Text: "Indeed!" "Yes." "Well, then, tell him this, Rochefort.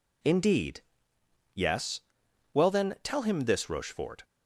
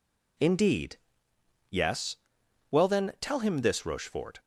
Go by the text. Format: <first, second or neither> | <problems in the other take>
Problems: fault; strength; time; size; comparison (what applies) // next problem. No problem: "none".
neither | none